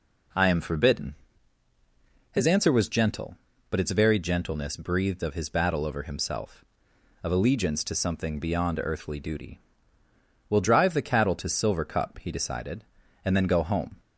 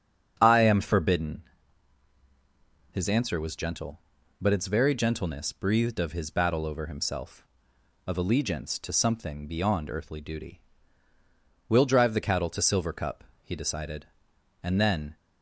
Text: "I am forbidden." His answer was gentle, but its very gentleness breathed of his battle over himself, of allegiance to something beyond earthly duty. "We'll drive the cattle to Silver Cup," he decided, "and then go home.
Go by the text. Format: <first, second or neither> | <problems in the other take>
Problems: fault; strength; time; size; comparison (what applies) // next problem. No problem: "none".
first | starts louder than the rest; strong; until 1.4 s; 7.5 dB // stops before "go home"; at 15.1 s